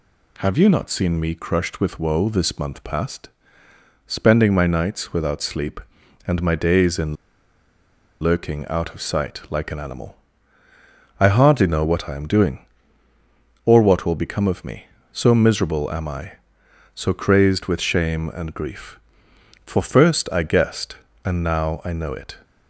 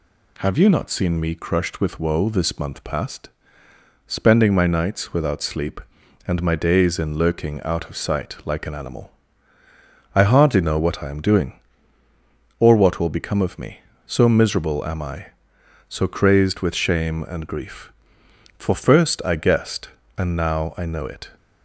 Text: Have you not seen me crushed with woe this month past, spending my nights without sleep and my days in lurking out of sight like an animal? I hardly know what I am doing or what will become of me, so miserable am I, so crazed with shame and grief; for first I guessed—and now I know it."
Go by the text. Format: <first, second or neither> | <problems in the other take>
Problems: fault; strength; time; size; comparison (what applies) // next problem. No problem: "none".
second | pauses between "in" and "lurking"; at 7.1 s; 1.0 s long